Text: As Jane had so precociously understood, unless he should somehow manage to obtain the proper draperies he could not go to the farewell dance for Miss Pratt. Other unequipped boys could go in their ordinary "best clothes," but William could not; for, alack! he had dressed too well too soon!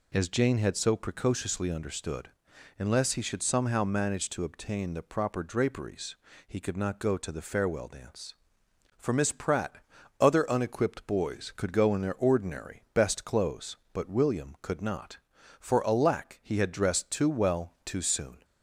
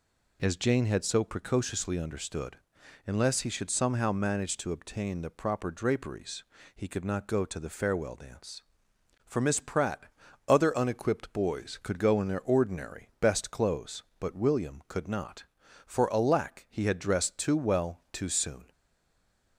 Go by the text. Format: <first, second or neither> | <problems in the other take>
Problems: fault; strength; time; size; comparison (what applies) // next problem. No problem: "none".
first | pauses between "draperies" and "he"; slight; at 6.4 s; 0.32 s long; slight in the first // stays silent after the last word; slight; from 18.7 s on; 0.8 s long